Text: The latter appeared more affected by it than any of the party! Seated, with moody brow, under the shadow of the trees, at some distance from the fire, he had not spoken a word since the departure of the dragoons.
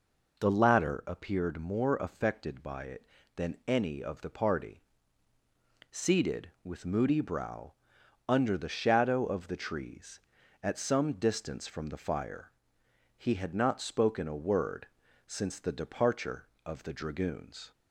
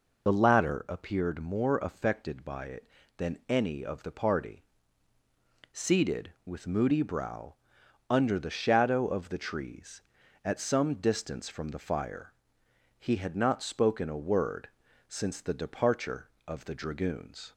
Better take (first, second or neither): first